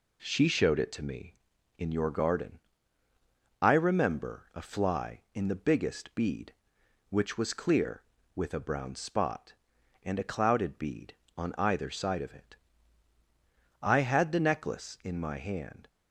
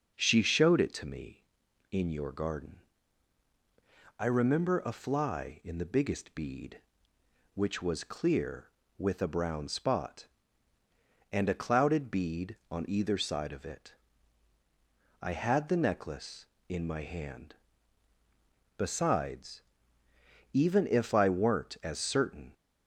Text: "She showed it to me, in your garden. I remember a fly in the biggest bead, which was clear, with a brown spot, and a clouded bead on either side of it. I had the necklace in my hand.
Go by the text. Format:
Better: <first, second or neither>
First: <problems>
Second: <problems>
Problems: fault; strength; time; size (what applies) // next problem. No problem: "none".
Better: first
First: none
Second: starts louder than the rest; noticeable; until 1.1 s; 6 dB // goes on to say "Besides even if I weren't as certain"; strong; from 18.7 s on; 3.7 s long